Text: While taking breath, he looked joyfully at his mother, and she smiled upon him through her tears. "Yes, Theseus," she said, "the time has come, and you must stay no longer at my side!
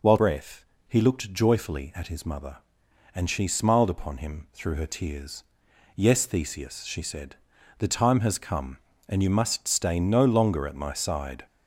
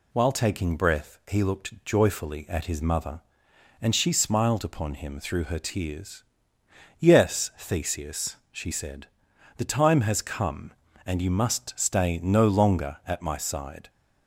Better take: second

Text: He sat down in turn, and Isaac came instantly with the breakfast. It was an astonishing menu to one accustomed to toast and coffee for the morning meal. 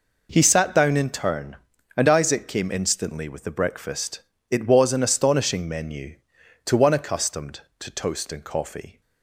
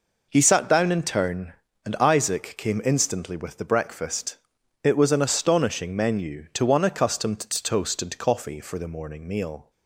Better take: second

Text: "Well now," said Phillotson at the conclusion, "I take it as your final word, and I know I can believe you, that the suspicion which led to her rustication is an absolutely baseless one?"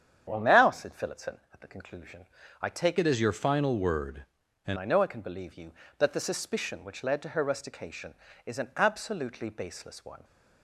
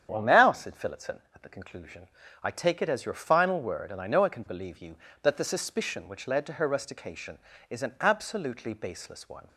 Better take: second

